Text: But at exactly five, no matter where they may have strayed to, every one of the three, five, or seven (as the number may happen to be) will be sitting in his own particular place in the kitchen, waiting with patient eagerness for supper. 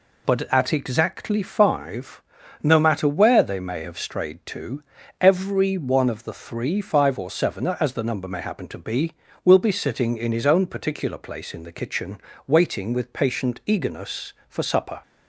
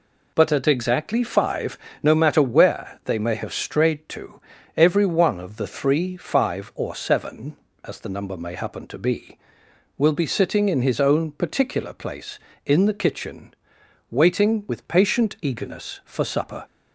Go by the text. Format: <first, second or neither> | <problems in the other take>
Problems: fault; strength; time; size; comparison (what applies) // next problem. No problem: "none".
neither | none